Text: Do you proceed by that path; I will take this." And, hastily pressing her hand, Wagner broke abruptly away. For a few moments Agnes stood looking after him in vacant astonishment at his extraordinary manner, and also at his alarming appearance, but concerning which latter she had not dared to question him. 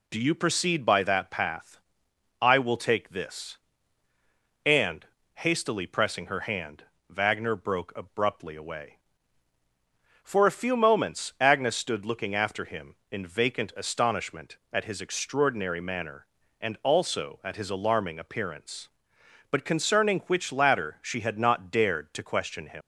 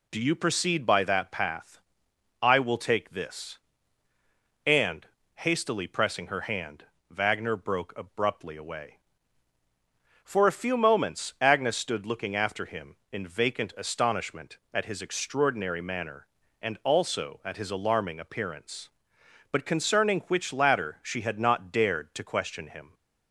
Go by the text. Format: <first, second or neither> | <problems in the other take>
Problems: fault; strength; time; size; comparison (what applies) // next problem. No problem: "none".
second | leaves "him" unfinished; at 22.8 s; 120 ms